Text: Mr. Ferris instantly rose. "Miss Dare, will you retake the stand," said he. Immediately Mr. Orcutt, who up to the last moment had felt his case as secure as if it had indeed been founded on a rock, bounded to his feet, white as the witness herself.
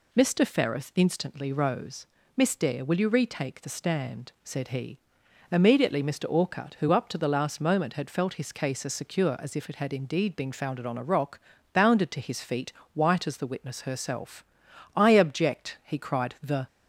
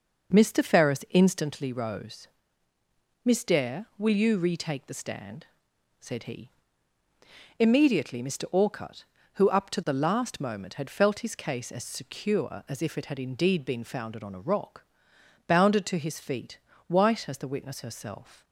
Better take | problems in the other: second | goes on to say "I object he cried The"; strong; from 14.9 s on; 1.7 s long

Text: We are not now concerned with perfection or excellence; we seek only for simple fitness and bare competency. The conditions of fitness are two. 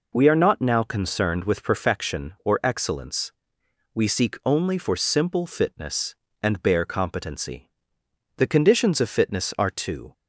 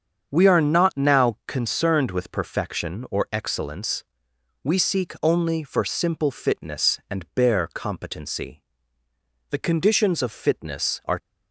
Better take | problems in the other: first | starts louder than the rest; strong; until 1.3 s; 7 dB // stops before "two"; at 11.1 s

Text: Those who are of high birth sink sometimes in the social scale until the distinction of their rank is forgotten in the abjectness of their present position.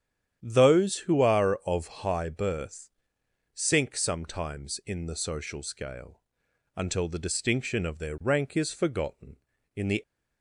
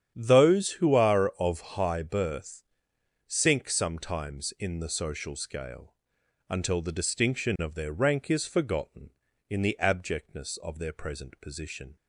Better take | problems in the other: second | starts louder than the rest; strong; until 1.4 s; 9.5 dB; strong in the second // pauses between "birth" and "sink"; noticeable; at 2.8 s; 0.64 s long; noticeable in the second // pauses between "scale" and "until"; noticeable; at 6.1 s; 0.56 s long; noticeable in the second // stops before "abjectness of their present position"; at 10.0 s

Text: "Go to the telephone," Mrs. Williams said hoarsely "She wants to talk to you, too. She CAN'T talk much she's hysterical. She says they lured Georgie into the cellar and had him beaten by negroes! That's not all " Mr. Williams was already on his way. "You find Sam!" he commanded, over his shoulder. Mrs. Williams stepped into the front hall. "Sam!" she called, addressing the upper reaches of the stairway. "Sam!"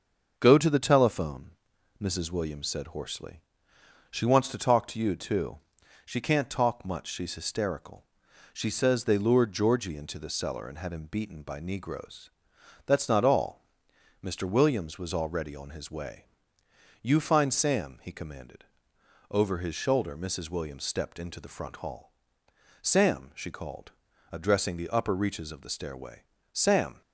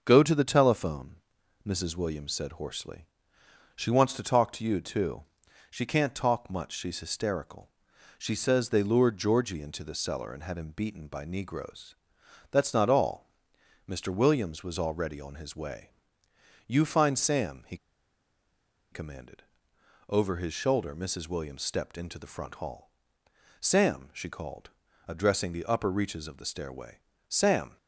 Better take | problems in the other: first | starts louder than the rest; until 1.0 s; 6.5 dB; also in the first // pauses between "hoarsely" and "She"; noticeable; at 3.0 s; 0.70 s long; noticeable in the first // pauses between "he" and "commanded"; at 17.7 s; 1.1 s long

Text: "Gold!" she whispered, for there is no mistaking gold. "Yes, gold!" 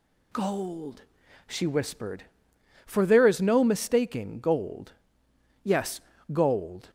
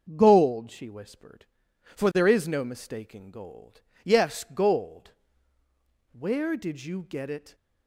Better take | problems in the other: first | starts louder than the rest; until 1.1 s; 6 dB // goes on to say "Where did you get it"; from 6.1 s on; 1.4 s long

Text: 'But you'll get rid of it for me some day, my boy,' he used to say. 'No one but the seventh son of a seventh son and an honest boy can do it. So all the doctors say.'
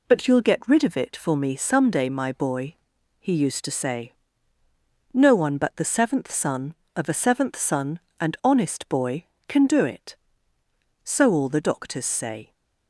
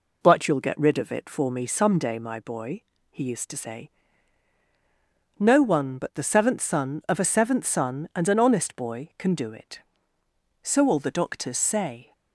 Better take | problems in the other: second | skips "an"; at 8.4 s

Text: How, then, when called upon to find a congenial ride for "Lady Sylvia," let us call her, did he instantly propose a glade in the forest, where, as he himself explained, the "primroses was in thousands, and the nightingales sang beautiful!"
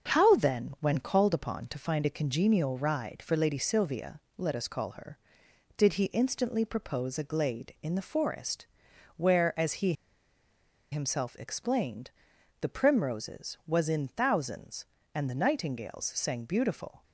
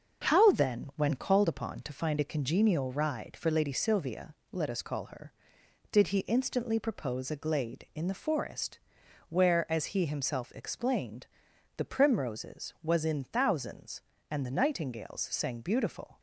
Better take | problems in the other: second | starts louder than the rest; until 1.1 s; 6.5 dB; also in the second // pauses between "he" and "himself"; noticeable; at 9.9 s; 0.97 s long

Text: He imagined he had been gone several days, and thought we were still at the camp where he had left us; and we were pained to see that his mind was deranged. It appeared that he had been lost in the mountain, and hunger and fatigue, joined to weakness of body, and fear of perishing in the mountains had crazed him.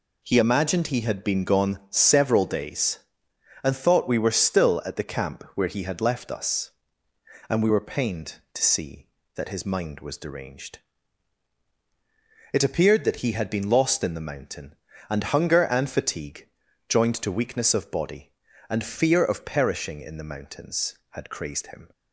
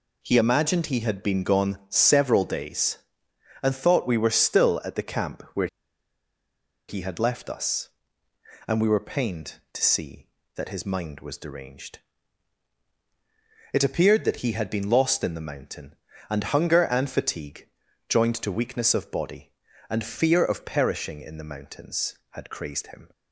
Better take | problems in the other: first | pauses between "where" and "he"; at 5.6 s; 1.2 s long

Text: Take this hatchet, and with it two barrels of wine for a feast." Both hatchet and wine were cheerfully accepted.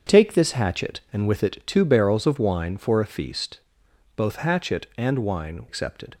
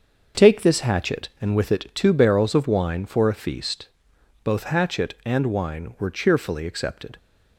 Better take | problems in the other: second | starts louder than the rest; until 1.2 s; 7 dB; also in the second // skips "were cheerfully"; at 5.6 s

